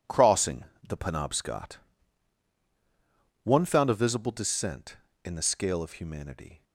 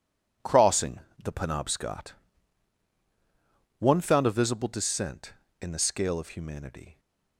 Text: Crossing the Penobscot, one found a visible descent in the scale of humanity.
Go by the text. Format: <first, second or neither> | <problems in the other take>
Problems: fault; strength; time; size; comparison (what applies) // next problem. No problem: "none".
neither | pauses between "Crossing" and "the"; slight; the same in both